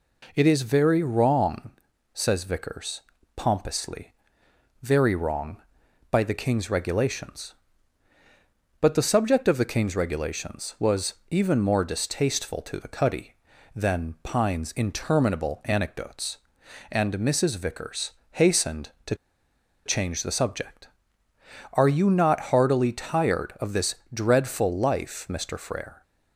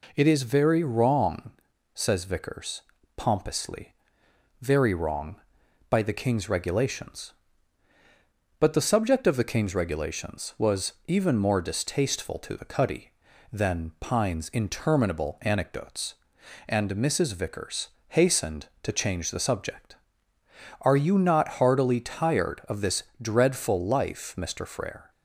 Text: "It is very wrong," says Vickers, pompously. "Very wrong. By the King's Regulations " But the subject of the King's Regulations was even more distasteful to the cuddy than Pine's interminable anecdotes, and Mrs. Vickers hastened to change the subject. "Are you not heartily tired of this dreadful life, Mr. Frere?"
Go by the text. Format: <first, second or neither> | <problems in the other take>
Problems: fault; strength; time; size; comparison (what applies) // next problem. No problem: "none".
second | pauses between "was" and "even"; slight; at 11.1 s; 0.16 s long // pauses between "Vickers" and "hastened"; slight; at 18.1 s; 0.22 s long; slight in the second // pauses between "to" and "change"; noticeable; at 19.1 s; 0.70 s long // pauses between "this" and "dreadful"; slight; at 23.9 s; 0.18 s long; slight in the second